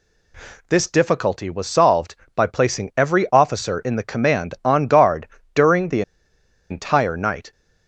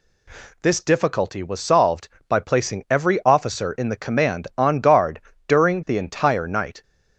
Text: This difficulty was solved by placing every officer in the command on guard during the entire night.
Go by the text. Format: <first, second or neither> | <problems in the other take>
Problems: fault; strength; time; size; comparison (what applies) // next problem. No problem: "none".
second | pauses between "guard" and "during"; slight; at 5.2 s; 0.26 s long; slight in the second // pauses between "the" and "entire"; noticeable; at 6.0 s; 0.69 s long